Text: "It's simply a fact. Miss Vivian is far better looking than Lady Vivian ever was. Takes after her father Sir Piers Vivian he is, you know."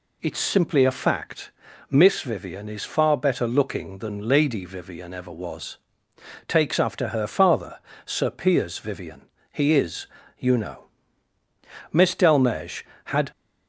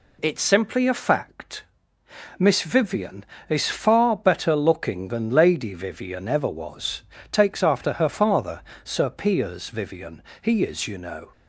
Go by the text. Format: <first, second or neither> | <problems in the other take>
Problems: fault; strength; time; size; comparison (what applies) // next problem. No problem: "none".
second | pauses between "father" and "Sir"; slight; at 7.7 s; 0.26 s long; slight in the second // pauses between "Vivian" and "he"; slight; at 9.2 s; 0.26 s long; slight in the second // goes on to say "Miss Delmege had"; from 11.9 s on; 1.4 s long